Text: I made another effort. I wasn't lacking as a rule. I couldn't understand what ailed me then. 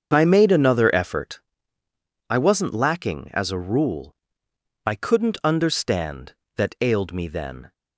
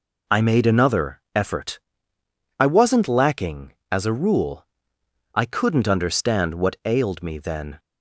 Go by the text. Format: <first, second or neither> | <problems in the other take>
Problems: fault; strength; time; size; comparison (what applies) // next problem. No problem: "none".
second | starts louder than the rest; until 1.1 s; 7 dB // says "that" for "what"; at 6.5 s